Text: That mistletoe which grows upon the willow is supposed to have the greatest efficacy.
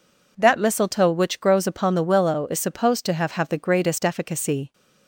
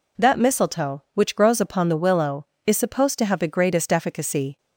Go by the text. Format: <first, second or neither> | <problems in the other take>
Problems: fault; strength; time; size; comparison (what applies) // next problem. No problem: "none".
second | says "have" twice; at 3.3 s